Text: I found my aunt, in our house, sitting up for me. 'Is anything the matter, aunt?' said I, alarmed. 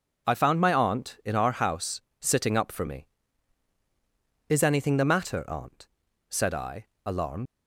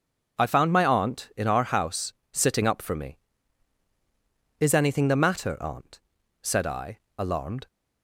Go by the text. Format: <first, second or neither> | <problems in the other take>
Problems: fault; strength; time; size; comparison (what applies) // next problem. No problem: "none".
second | leaves "alarmed" unfinished; at 7.4 s; 85 ms